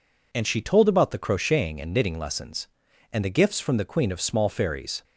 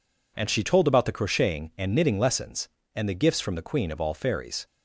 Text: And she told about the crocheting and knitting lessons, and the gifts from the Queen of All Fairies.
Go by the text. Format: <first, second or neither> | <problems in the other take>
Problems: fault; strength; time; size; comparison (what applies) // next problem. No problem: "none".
second | says "Small" for "All"; at 4.2 s